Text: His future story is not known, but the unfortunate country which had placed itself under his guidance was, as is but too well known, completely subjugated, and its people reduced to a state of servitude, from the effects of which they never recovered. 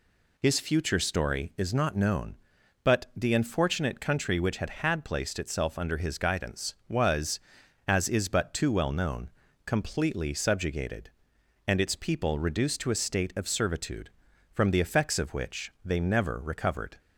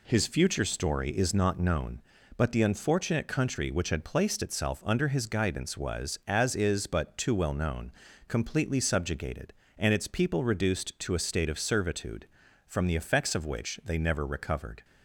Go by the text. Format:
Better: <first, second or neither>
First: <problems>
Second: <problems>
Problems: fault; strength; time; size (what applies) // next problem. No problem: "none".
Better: second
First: says "had" twice; at 4.6 s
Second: none